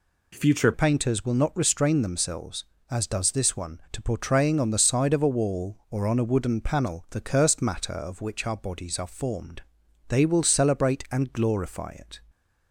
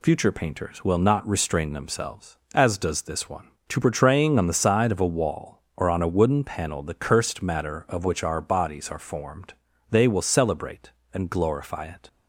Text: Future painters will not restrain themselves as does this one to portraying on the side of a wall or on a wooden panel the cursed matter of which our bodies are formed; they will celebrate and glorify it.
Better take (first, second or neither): second